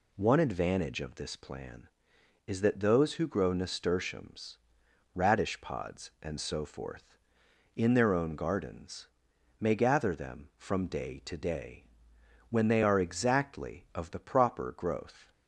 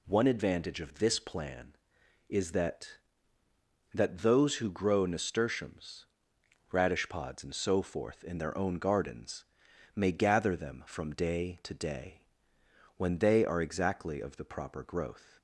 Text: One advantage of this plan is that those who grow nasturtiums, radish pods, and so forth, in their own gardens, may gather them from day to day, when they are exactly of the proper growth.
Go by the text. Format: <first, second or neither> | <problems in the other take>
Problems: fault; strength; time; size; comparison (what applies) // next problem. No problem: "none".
first | says "that" twice; at 3.9 s